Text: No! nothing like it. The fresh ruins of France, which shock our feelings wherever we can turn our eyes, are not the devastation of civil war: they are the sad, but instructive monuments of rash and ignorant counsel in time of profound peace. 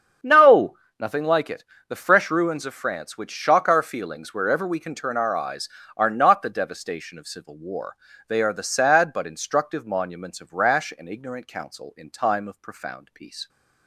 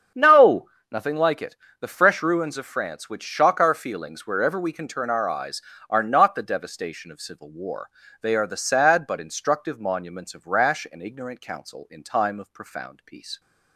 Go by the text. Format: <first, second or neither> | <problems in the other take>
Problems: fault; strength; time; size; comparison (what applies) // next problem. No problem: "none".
neither | starts louder than the rest; the same in both